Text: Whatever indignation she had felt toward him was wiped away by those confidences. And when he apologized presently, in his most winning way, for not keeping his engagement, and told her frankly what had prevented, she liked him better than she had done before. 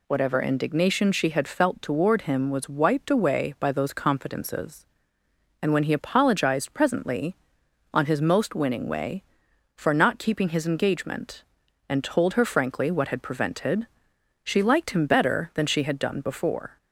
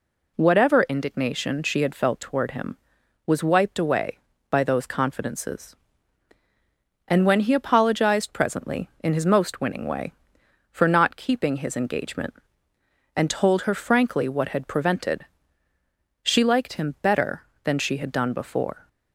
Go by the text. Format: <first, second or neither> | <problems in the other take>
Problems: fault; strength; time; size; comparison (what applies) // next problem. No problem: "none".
second | says "on" for "in"; at 7.9 s